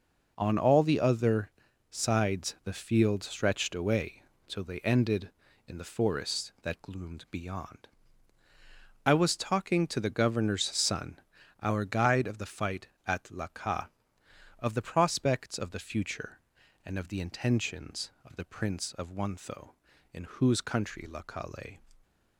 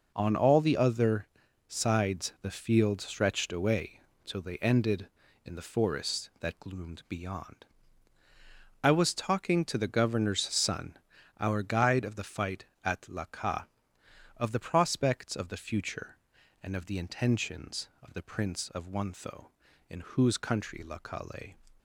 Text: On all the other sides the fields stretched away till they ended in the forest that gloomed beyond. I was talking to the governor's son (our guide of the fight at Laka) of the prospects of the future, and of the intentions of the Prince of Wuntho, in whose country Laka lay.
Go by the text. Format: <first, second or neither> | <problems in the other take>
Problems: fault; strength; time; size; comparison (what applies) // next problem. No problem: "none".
neither | pauses between "other" and "sides"; the same in both // pauses between "away" and "till"; slight; the same in both